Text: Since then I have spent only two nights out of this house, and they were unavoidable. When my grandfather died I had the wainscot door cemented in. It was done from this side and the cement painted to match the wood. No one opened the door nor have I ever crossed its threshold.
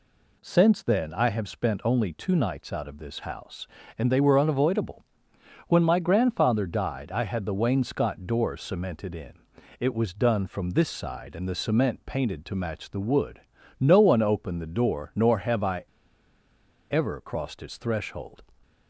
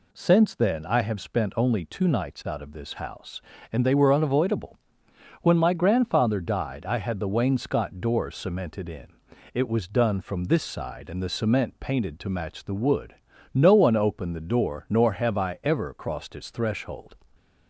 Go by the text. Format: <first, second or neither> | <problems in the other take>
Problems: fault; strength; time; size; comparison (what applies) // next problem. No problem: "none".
second | pauses between "I" and "ever"; at 15.8 s; 1.0 s long